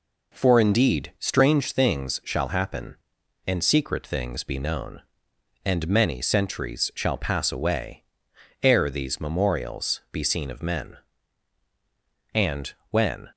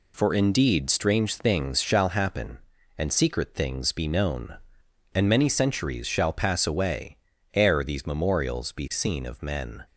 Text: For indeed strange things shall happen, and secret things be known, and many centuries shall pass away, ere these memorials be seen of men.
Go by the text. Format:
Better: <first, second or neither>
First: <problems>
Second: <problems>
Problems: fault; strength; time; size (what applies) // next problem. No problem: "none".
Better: second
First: goes on to say "And when"; noticeable; from 12.3 s on; 0.98 s long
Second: none